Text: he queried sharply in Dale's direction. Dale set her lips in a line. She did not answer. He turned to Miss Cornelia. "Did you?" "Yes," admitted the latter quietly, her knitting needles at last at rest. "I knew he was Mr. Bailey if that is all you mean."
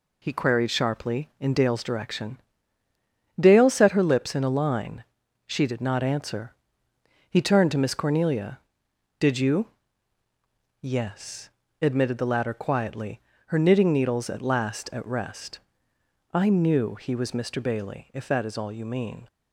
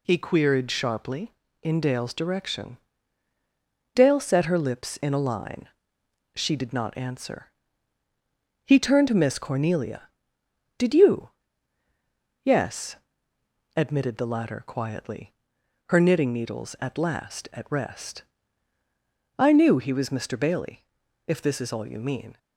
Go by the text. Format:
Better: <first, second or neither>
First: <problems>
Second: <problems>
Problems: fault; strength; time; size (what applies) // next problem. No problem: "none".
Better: first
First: none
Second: pauses between "Bailey" and "if"; at 20.8 s; 0.42 s long // says "this" for "that"; at 21.4 s